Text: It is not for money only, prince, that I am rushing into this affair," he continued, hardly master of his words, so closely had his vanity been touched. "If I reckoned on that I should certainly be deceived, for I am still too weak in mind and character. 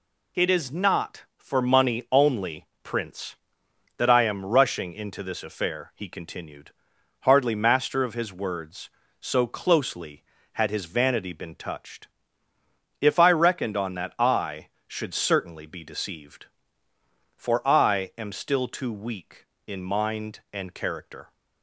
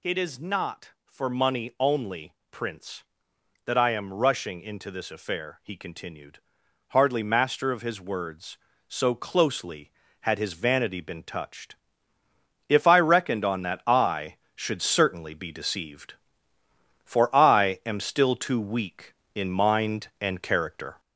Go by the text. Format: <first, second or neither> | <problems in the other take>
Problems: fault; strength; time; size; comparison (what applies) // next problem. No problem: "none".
first | gets louder; noticeable; throughout; 4 dB